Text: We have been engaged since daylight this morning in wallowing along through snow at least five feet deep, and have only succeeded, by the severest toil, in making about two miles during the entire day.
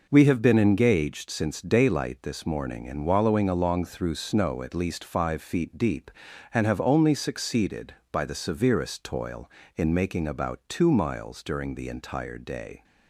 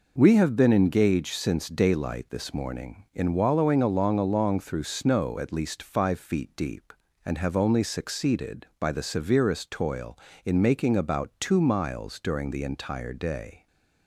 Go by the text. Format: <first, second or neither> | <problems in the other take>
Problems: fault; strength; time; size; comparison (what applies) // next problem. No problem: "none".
first | says "along" twice; at 4.1 s // stays silent after the last word; slight; from 13.5 s on; 0.5 s long